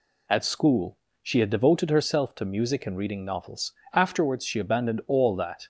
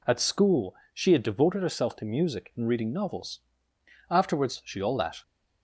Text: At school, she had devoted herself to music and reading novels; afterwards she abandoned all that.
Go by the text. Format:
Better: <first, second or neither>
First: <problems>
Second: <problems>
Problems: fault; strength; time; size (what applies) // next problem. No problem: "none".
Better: first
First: none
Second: skips "abandoned"; at 4.8 s